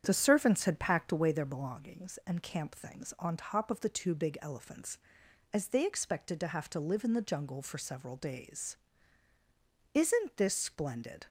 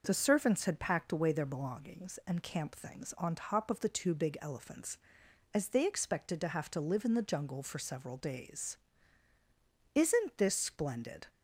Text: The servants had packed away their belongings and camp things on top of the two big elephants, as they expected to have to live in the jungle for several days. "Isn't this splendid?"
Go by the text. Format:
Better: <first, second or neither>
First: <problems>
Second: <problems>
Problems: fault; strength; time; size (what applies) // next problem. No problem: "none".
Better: second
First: starts louder than the rest; strong; until 1.5 s; 8 dB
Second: none